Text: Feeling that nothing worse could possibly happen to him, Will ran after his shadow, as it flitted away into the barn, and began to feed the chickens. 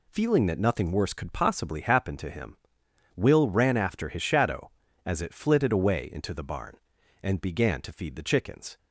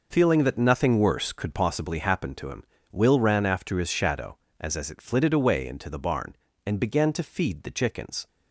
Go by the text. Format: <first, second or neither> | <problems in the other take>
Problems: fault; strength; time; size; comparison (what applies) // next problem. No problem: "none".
first | says "as" twice; at 4.7 s